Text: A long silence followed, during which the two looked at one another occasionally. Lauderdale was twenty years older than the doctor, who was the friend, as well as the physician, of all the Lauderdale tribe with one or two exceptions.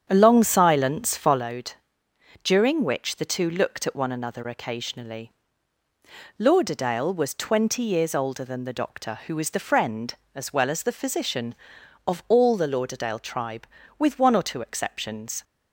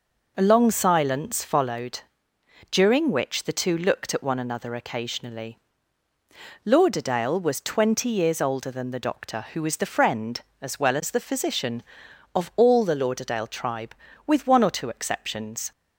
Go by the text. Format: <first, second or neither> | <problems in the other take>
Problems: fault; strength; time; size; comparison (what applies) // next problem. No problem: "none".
second | starts louder than the rest; strong; until 1.4 s; 8 dB